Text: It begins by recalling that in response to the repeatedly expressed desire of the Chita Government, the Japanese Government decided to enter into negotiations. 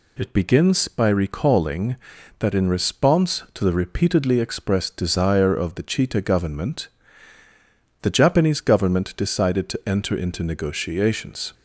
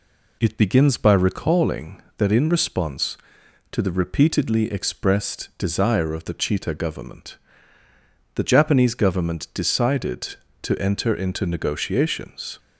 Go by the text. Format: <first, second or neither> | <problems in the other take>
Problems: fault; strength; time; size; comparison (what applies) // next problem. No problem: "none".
neither | none